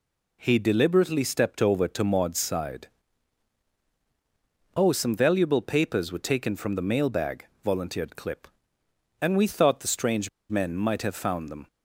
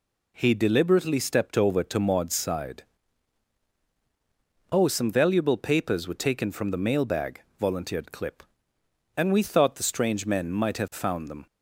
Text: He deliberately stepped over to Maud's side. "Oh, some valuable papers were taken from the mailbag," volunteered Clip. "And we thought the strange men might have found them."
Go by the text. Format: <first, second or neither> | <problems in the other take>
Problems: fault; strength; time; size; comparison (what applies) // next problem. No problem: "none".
second | pauses between "strange" and "men"; slight; at 10.2 s; 0.21 s long